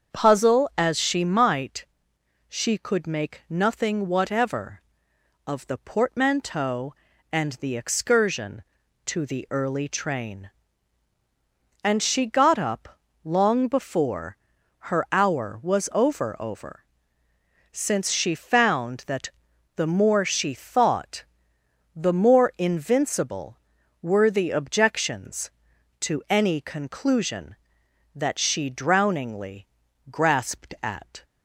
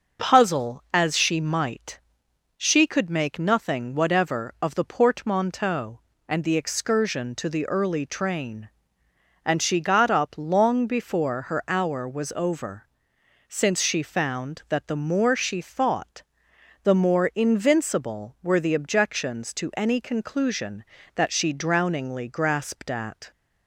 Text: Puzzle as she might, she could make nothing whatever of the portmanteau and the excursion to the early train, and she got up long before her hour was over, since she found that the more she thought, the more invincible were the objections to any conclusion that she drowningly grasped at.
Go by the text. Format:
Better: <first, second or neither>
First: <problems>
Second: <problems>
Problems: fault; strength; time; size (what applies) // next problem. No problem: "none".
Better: second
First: starts louder than the rest; until 1.1 s; 7 dB // pauses between "up" and "long"; slight; at 12.9 s; 0.24 s long // pauses between "before" and "her"; at 14.3 s; 0.42 s long // says "over" twice; at 16.3 s // pauses between "that" and "the"; noticeable; at 19.2 s; 0.48 s long // pauses between "drowningly" and "grasped"; at 29.6 s; 0.44 s long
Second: none